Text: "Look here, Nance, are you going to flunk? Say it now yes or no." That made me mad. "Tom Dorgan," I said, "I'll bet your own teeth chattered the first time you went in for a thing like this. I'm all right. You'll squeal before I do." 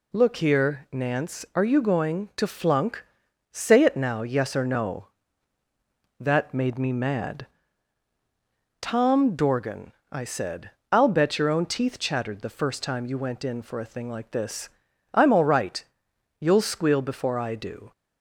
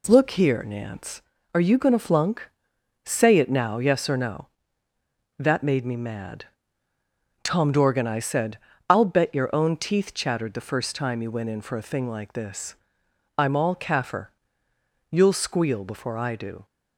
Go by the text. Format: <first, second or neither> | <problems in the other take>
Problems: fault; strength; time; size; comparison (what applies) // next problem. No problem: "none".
first | says "kaffir" for "right"; at 13.7 s